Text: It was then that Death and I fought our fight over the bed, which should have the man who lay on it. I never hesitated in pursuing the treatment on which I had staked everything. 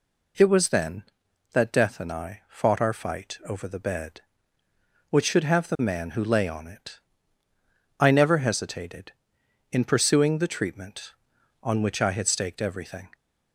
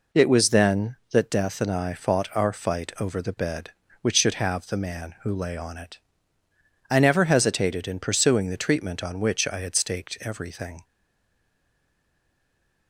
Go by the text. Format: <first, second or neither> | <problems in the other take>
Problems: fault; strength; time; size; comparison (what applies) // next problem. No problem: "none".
first | stays silent after the last word; noticeable; from 10.8 s on; 2.0 s long